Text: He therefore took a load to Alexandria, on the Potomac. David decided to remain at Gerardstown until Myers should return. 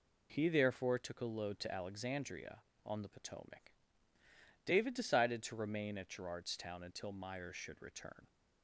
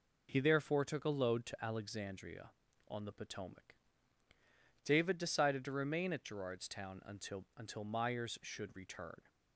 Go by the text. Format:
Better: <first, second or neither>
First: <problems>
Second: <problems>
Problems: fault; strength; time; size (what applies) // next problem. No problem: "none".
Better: first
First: none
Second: says "until" twice; at 7.5 s